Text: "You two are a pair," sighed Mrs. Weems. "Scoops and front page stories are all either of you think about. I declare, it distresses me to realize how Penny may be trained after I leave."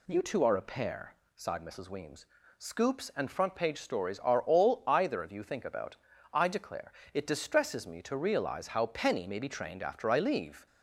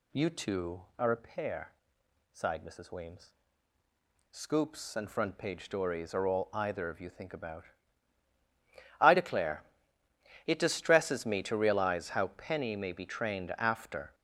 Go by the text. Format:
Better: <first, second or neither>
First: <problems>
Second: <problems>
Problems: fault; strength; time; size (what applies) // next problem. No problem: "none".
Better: first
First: none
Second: stops before "I leave"; at 14.1 s